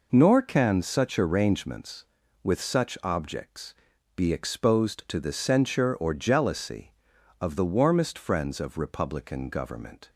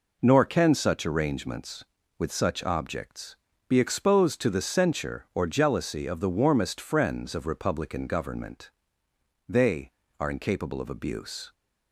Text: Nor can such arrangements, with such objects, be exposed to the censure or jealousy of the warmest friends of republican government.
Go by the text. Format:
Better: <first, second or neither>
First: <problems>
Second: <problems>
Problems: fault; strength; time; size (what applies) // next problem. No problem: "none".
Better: first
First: none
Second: goes on to say "They are incapable of abuse"; strong; from 9.4 s on; 2.0 s long